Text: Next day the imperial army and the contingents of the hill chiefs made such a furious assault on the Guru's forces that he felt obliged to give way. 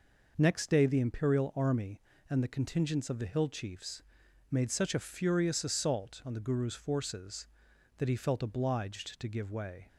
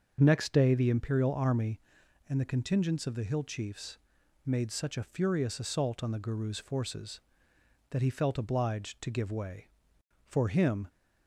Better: first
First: pauses between "chiefs" and "made"; noticeable; at 4.0 s; 0.50 s long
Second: starts louder than the rest; until 1.2 s; 6.5 dB // pauses between "chiefs" and "made"; noticeable; at 3.9 s; 0.48 s long // goes on to say "For him"; noticeable; from 10.2 s on; 0.62 s long

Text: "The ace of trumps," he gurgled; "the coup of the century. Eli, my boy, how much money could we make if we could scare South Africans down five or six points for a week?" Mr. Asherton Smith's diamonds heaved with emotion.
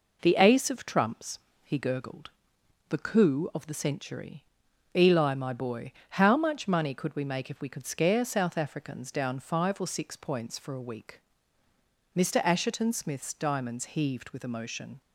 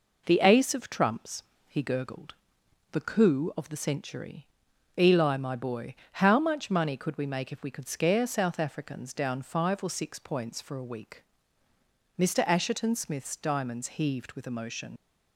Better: first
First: none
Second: leaves "emotion" unfinished; at 14.9 s; 70 ms

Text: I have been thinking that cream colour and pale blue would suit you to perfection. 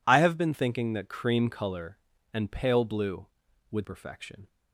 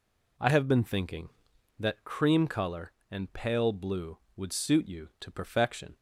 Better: second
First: skips "suit you to"; at 3.8 s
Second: none

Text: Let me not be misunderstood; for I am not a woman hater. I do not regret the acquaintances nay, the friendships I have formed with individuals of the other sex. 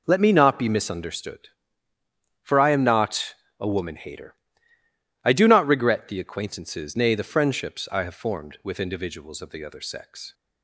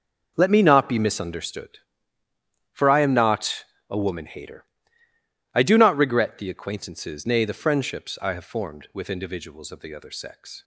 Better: first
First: pauses between "not" and "a"; slight; at 3.3 s; 0.22 s long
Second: gets quieter; strong; throughout; 12.5 dB // pauses between "not" and "a"; slight; at 3.6 s; 0.22 s long

